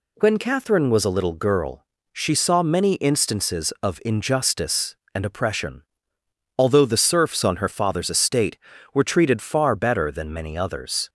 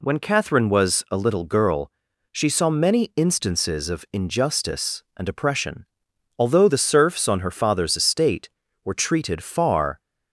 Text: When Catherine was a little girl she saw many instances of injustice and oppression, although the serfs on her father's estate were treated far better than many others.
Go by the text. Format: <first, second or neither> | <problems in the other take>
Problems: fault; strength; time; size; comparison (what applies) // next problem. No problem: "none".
first | pauses between "girl" and "she"; at 1.9 s; 0.40 s long; slight in the first // stops before "better than many others"; at 9.9 s